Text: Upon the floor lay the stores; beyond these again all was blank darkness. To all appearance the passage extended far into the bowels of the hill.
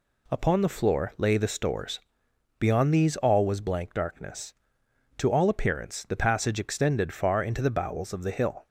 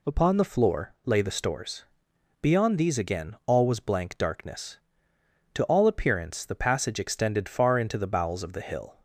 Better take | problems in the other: second | skips "again"; at 3.1 s

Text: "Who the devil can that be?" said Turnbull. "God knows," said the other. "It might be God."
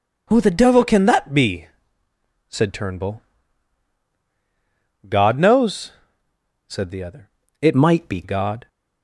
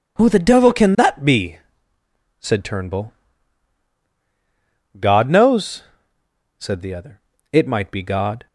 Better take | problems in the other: second | changes voice from "might" to "be"; from 7.7 to 8.2 s; 0.5 s long

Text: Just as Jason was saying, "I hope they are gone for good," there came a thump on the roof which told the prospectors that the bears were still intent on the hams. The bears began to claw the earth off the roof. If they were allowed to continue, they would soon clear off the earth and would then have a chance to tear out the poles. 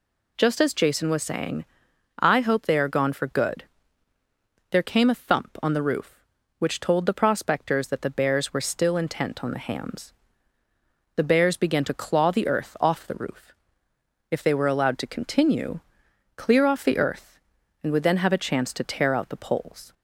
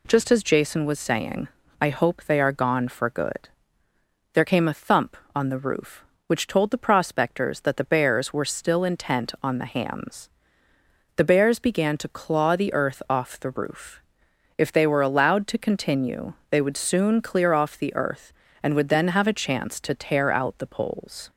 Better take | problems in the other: second | skips "they would soon"; at 16.0 s

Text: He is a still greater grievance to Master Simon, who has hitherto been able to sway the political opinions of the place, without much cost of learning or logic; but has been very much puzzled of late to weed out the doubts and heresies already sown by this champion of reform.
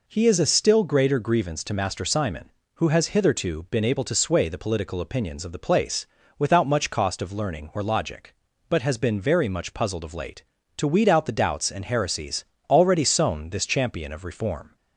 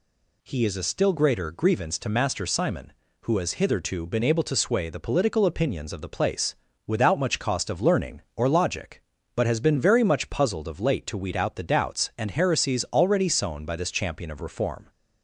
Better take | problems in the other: second | pauses between "heresies" and "already"; slight; at 12.4 s; 0.26 s long // skips "by"; at 13.5 s

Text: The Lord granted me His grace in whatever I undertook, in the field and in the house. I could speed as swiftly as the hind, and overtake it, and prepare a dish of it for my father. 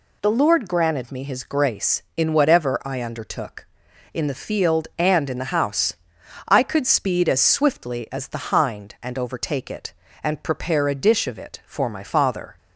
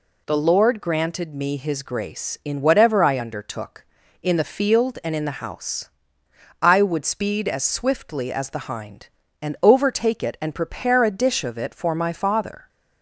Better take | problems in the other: first | says "would" for "could"; at 6.8 s

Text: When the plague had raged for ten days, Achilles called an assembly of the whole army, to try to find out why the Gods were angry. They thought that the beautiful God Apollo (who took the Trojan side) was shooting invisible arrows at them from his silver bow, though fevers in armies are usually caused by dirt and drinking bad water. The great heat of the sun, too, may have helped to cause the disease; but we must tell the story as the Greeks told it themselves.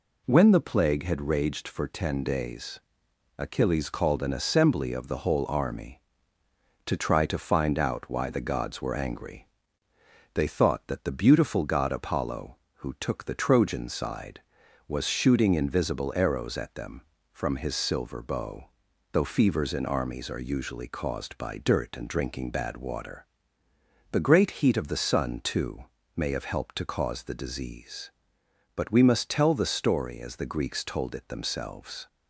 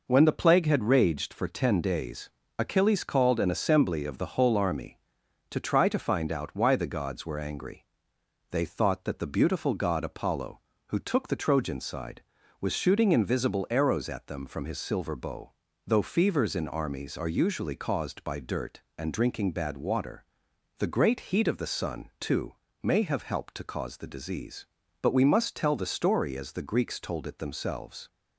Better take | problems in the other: neither | none

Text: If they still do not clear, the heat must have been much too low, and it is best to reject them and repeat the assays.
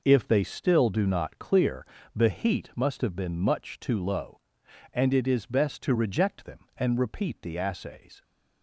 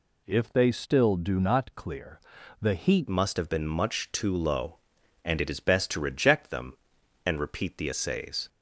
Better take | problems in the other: first | changes voice at "must"; from 3.0 s on; 5.4 s long

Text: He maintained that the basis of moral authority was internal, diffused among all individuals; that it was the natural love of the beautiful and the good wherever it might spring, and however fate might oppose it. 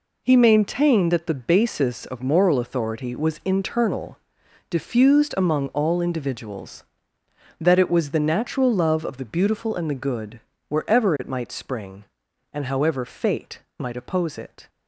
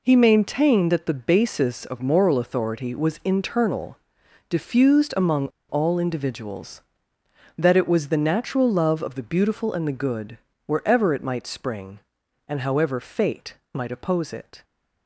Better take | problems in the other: first | pauses between "among" and "all"; slight; at 5.4 s; 0.21 s long // pauses between "good" and "wherever"; slight; at 10.3 s; 0.26 s long; slight in the first // pauses between "fate" and "might"; slight; at 13.5 s; 0.16 s long; slight in the first

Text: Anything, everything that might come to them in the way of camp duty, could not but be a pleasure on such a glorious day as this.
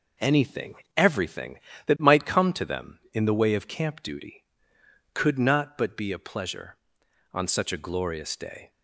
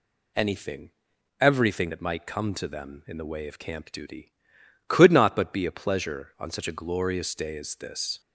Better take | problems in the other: second | stops before "as this"; at 8.7 s

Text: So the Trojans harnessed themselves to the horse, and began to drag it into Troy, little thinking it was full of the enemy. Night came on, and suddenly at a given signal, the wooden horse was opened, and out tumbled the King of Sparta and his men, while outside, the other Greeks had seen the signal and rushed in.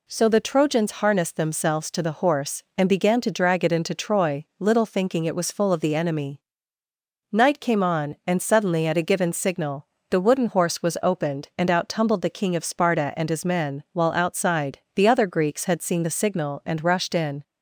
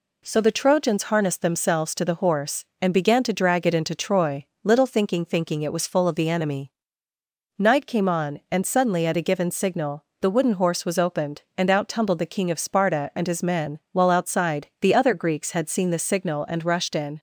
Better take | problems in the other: first | says "thinking" twice; at 5.2 s

